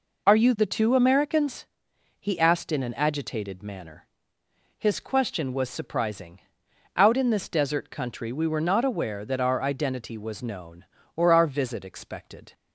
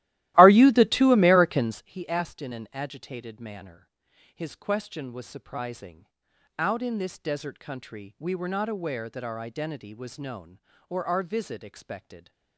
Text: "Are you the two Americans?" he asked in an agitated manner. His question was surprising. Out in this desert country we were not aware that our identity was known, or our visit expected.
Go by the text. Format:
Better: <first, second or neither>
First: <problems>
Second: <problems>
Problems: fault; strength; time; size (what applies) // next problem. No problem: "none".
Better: first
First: none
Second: starts louder than the rest; strong; until 1.9 s; 16 dB